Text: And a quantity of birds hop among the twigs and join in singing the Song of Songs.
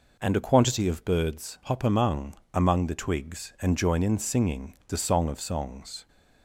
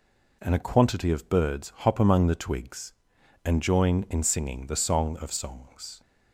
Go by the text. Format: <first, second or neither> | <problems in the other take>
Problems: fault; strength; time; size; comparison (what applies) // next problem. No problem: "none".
second | says "among" twice; at 2.5 s